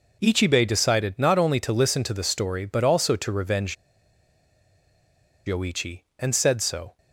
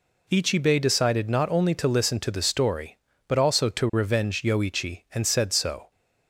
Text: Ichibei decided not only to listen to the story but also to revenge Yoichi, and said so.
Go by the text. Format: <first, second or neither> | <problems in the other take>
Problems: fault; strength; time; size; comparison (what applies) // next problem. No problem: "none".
second | pauses between "revenge" and "Yoichi"; strong; at 3.7 s; 1.7 s long